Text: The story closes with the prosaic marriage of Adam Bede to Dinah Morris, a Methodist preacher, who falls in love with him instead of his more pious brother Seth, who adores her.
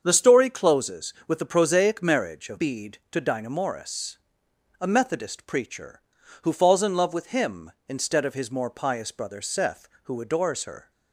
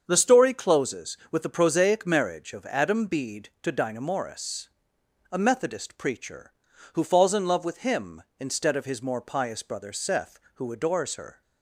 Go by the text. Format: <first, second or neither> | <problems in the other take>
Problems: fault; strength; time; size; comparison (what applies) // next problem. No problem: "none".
second | starts louder than the rest; strong; until 1.0 s; 7 dB; also in the second // skips "Adam"; at 2.5 s